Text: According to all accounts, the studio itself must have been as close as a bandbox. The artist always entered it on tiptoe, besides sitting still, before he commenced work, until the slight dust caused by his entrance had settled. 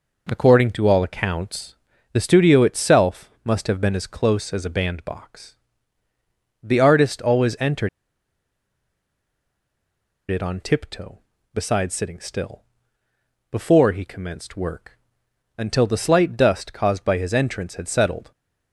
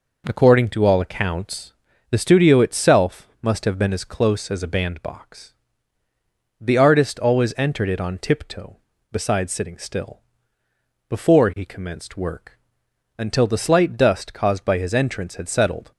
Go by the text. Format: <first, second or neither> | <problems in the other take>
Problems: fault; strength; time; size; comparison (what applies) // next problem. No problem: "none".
second | pauses between "itself" and "must"; slight; at 3.2 s; 0.16 s long; slight in the second // pauses between "entered" and "it"; strong; at 7.8 s; 2.4 s long